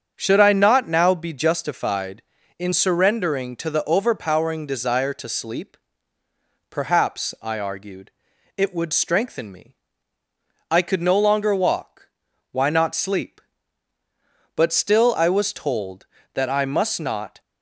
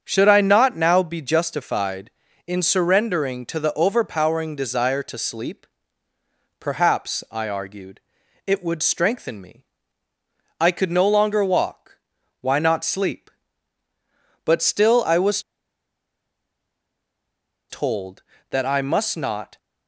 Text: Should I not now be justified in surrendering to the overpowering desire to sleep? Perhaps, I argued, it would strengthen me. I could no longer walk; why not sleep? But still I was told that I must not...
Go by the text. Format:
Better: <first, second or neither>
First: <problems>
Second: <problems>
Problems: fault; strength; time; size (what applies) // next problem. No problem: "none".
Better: first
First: starts louder than the rest; strong; until 1.1 s; 7 dB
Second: starts louder than the rest; strong; until 1.0 s; 7 dB // pauses between "was" and "told"; strong; at 15.4 s; 2.2 s long